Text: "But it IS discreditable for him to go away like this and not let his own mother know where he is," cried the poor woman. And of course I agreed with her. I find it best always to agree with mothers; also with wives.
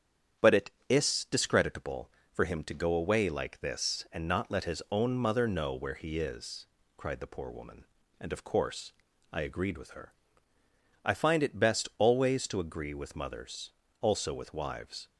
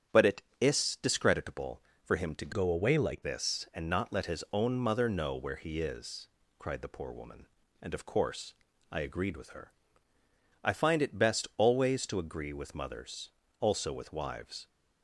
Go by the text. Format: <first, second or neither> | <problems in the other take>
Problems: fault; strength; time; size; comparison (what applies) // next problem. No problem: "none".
first | starts louder than the rest; strong; until 1.3 s; 9 dB; strong in the first // changes voice from "go" to "like"; from 2.5 to 3.2 s; 0.7 s long // pauses between "course" and "I"; at 8.5 s; 0.38 s long; also in the first